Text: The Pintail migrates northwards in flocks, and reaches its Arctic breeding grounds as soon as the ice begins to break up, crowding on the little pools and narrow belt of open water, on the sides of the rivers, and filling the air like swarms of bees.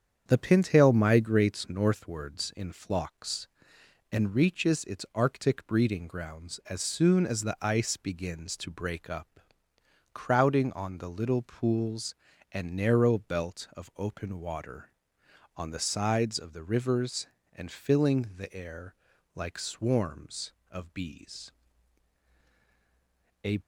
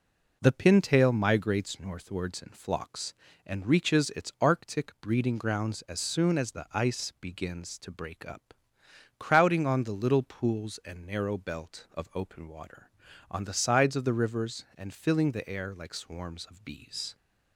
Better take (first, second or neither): second